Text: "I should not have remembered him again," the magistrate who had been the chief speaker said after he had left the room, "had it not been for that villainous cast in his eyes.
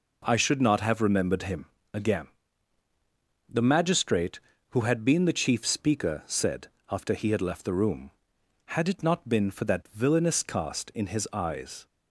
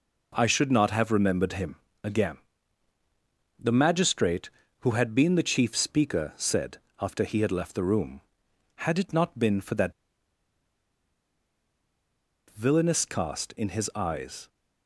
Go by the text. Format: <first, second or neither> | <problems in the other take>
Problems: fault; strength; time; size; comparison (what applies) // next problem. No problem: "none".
first | pauses between "him" and "again"; slight; at 1.7 s; 0.28 s long; slight in the first // pauses between "said" and "after"; slight; at 6.7 s; 0.20 s long; slight in the first // pauses between "that" and "villainous"; strong; at 9.9 s; 2.5 s long